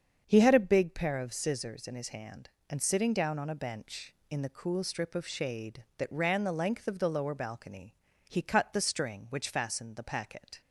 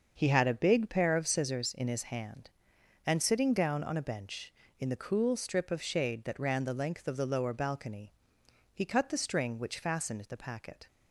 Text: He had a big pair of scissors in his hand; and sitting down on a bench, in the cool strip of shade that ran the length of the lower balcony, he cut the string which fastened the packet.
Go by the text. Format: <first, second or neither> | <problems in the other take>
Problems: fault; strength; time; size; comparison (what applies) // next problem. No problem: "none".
neither | starts louder than the rest; the same in both